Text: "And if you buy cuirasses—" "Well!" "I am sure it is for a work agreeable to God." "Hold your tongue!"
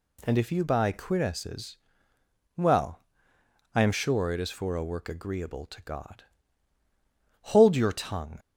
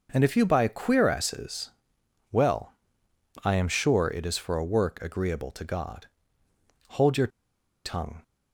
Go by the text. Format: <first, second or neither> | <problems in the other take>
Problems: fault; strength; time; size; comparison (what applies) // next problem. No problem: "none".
first | pauses between "your" and "tongue"; noticeable; at 7.2 s; 0.56 s long